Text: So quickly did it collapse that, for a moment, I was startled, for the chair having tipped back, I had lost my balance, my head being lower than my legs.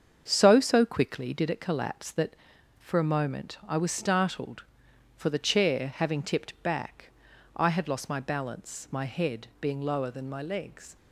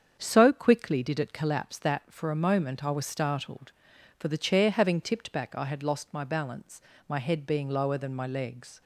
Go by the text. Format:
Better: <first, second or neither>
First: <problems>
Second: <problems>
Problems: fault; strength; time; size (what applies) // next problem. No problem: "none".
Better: second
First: starts louder than the rest; strong; until 1.2 s; 7 dB // says "So" twice; at 0.5 s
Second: starts louder than the rest; strong; until 1.1 s; 7.5 dB